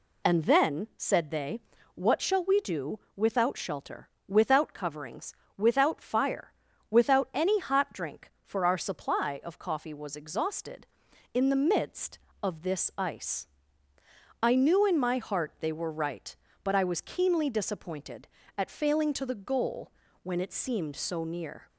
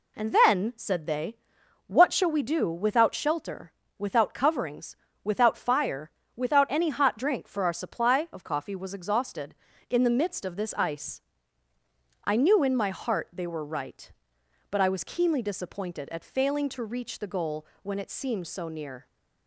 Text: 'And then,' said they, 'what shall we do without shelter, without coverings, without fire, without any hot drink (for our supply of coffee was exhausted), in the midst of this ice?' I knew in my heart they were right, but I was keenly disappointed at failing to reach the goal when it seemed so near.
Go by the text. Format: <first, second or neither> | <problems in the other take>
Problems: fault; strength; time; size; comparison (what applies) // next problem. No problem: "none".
second | pauses between "do" and "without"; slight; at 2.9 s; 0.18 s long // skips "reach"; at 19.2 s // pauses between "goal" and "when"; slight; at 19.9 s; 0.30 s long; slight in the second